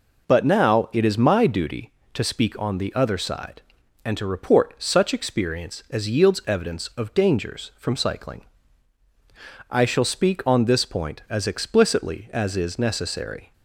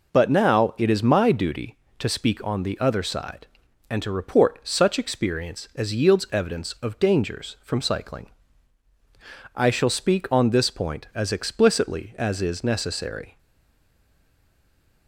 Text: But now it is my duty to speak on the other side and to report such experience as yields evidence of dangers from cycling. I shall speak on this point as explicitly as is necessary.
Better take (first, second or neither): first